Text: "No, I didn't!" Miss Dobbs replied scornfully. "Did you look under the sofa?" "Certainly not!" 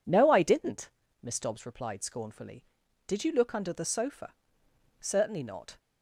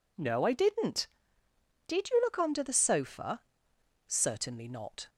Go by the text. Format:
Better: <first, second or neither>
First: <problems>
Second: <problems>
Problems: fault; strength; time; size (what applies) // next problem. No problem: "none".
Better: first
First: none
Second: skips "Miss Dobbs replied scornfully"; at 1.4 s